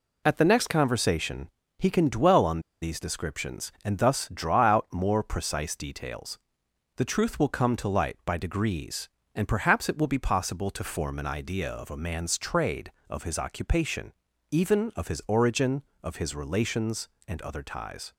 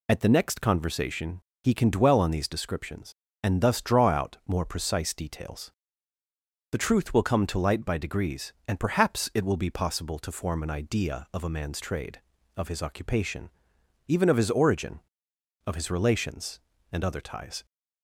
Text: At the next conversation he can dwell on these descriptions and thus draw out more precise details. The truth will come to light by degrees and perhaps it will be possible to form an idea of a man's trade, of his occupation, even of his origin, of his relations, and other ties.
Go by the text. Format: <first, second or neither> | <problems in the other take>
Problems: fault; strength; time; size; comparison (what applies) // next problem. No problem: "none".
second | pauses between "conversation" and "he"; slight; at 1.4 s; 0.28 s long; slight in the second // pauses between "on" and "these"; slight; at 2.5 s; 0.22 s long